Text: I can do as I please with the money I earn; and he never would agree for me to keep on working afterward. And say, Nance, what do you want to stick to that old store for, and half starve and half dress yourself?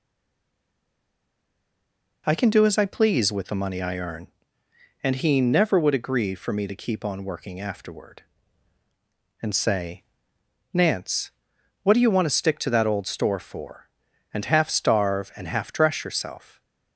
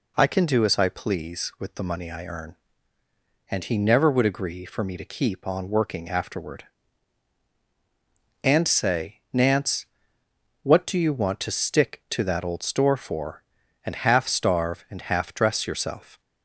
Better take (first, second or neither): second